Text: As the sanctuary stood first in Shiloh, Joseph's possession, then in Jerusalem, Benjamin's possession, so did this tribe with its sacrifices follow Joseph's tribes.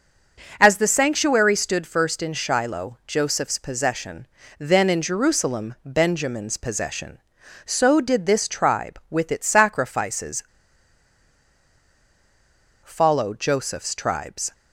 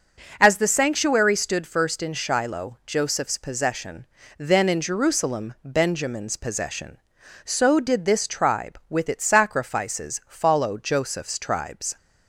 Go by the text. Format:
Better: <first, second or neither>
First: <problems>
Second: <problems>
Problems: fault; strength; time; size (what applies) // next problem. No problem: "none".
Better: second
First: pauses between "sacrifices" and "follow"; strong; at 10.4 s; 2.4 s long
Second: none